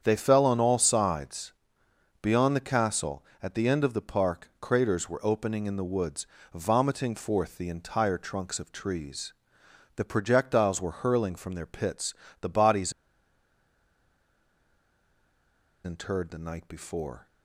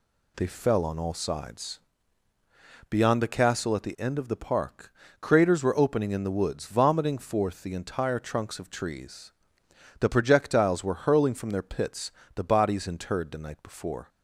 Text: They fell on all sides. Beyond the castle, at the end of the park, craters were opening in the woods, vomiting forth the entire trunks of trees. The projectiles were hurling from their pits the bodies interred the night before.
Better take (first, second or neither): second